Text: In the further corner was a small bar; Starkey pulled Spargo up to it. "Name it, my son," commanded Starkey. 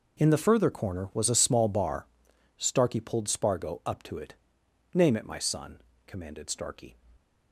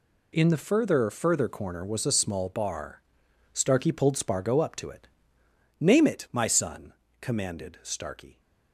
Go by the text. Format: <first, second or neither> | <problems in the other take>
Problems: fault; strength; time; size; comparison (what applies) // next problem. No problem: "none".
first | says "further" twice; at 1.1 s